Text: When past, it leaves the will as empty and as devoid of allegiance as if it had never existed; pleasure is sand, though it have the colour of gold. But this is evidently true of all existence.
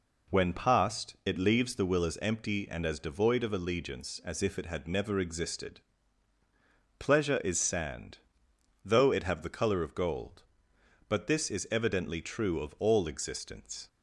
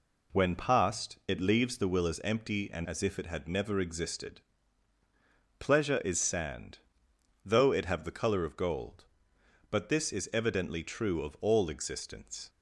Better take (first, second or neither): first